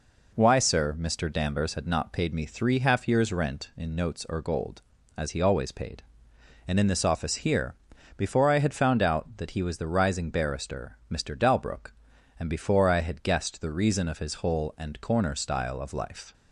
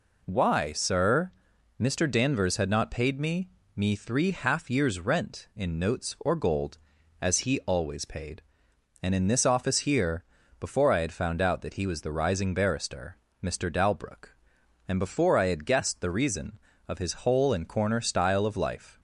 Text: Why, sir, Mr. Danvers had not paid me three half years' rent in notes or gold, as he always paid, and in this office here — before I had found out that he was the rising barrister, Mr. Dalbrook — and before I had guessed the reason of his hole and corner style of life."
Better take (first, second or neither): first